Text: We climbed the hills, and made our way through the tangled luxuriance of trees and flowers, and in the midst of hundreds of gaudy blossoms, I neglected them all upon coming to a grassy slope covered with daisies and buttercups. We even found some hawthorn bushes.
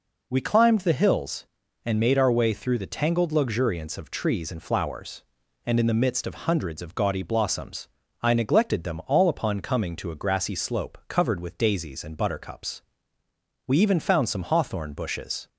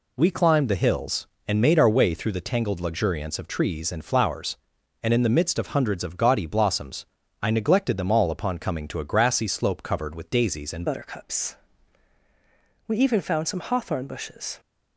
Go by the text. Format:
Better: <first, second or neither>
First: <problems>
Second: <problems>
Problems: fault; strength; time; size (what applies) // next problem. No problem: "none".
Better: first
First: none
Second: changes voice at "buttercups"; from 10.8 s on; 3.7 s long